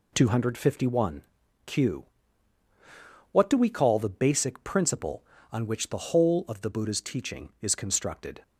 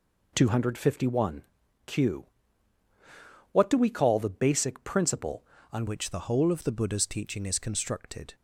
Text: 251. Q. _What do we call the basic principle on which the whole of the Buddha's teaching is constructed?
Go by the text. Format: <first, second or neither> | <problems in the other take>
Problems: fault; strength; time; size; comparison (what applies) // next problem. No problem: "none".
first | changes voice at "which"; from 5.8 s on; 2.5 s long